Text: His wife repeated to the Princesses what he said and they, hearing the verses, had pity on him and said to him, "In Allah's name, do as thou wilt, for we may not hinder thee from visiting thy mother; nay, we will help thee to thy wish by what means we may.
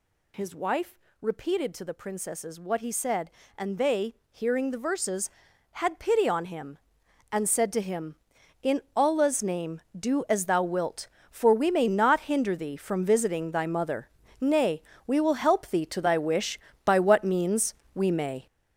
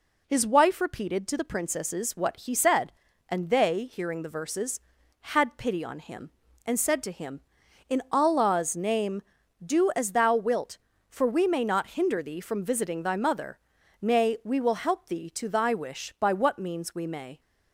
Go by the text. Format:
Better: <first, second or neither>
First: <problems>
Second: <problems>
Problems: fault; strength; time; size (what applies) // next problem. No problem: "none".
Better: second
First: gets louder; strong; throughout; 8 dB // pauses between "wife" and "repeated"; slight; at 0.9 s; 0.22 s long // pauses between "means" and "we"; slight; at 17.7 s; 0.20 s long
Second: none